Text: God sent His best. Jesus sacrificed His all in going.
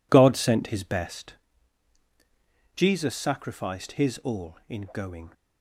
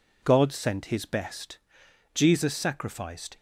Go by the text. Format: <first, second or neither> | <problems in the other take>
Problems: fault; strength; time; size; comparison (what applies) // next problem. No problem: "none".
first | stops before "His all in going"; at 3.3 s